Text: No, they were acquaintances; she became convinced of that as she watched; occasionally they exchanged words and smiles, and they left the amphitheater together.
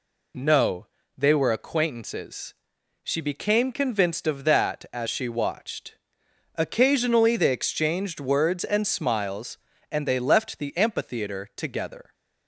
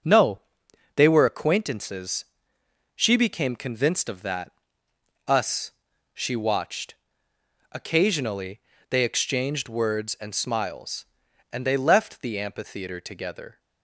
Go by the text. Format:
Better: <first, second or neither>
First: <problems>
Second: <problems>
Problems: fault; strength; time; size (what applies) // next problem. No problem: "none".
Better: first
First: none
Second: says "us" for "as"; at 5.2 s // pauses between "occasionally" and "they"; slight; at 8.5 s; 0.30 s long